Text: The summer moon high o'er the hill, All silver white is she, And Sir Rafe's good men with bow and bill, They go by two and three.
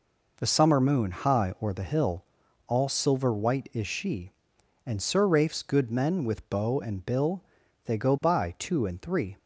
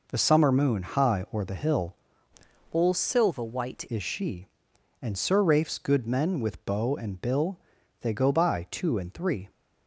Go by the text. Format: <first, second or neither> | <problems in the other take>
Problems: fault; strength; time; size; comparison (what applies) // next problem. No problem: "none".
first | changes voice from "All" to "white"; from 2.7 to 3.8 s; 1.1 s long